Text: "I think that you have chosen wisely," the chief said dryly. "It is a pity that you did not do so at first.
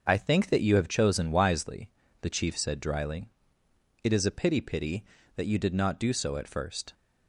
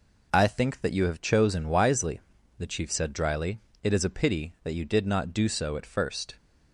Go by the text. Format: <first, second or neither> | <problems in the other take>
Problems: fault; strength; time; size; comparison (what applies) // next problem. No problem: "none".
second | starts louder than the rest; until 1.0 s; 6.5 dB // says "pity" twice; at 4.6 s